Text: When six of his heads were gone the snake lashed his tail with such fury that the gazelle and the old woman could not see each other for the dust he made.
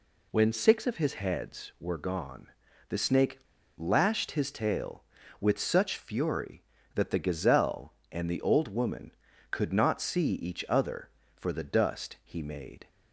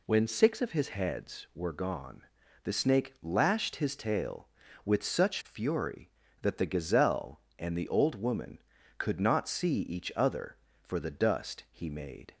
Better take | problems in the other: second | pauses between "gone" and "the"; at 2.4 s; 0.40 s long; also in the second // pauses between "snake" and "lashed"; at 3.3 s; 0.38 s long

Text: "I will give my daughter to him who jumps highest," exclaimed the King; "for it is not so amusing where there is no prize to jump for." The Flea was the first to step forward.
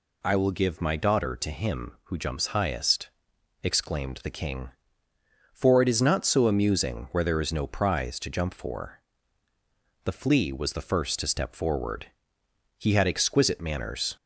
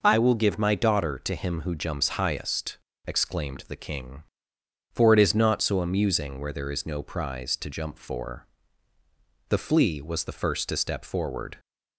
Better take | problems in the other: second | goes on to say "He had exquisite manners"; from 12.7 s on; 1.3 s long

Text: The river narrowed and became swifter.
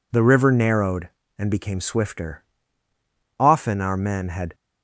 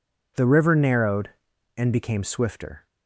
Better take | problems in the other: second | goes on to say "Often our men had"; noticeable; from 3.4 s on; 1.1 s long

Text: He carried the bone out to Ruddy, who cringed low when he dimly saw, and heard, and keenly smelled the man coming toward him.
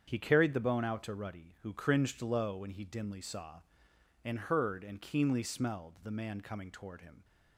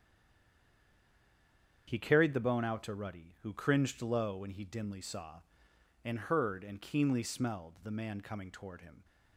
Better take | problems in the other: first | stays silent before the first word; noticeable; until 1.8 s; 1.8 s long // starts louder than the rest; strong; until 2.8 s; 7.5 dB; strong in the first

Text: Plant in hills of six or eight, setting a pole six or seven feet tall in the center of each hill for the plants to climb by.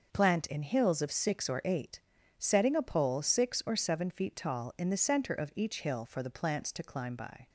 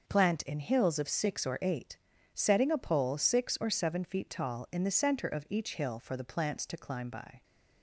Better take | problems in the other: neither | none

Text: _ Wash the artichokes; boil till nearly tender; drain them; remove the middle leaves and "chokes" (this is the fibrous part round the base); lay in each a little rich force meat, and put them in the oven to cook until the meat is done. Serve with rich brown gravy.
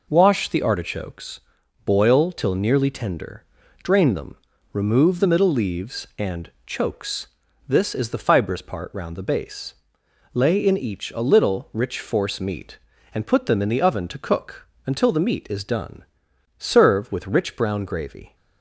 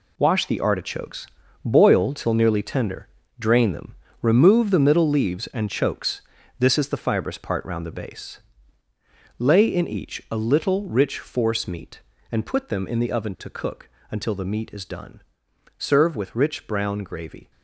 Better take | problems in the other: first | gets quieter; strong; throughout; 10 dB // pauses between "cook" and "until"; slight; at 13.9 s; 0.20 s long; slight in the first

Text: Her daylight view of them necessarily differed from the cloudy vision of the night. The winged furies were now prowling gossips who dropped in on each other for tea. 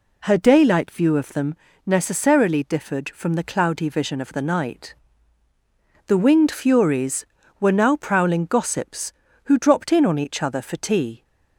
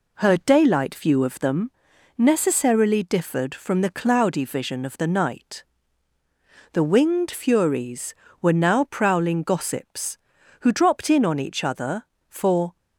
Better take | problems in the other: first | pauses between "them" and "necessarily"; noticeable; at 1.7 s; 0.46 s long; slight in the first // stops before "tea"; at 12.7 s

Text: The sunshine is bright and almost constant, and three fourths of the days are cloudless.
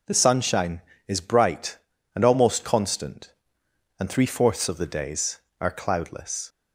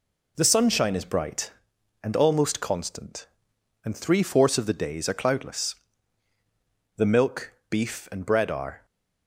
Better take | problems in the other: first | goes on to say "The milk beef and bread are"; strong; from 6.9 s on; 1.8 s long

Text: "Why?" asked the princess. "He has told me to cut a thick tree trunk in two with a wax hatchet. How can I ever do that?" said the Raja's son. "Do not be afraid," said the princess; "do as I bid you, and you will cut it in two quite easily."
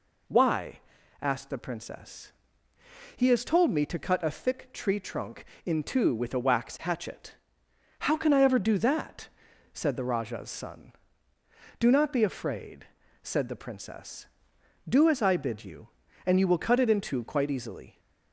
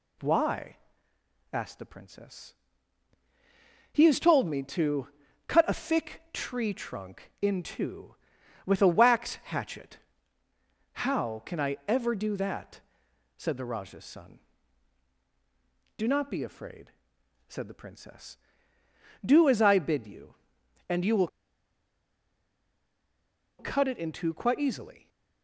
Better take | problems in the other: first | pauses between "to" and "cut"; at 5.0 s; 0.38 s long // pauses between "will" and "cut"; strong; at 21.2 s; 2.3 s long

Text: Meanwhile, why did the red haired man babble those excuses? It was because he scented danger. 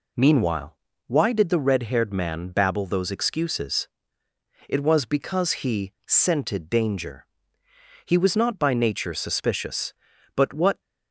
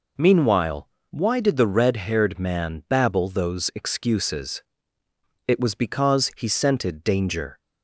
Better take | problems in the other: second | goes on to say "He was not by nature suspicious but what"; strong; from 8.0 s on; 2.7 s long

